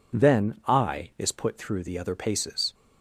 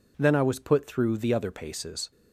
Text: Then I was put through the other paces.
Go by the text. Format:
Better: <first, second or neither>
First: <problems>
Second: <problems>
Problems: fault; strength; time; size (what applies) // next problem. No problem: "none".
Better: second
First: says "is" for "was"; at 1.1 s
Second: none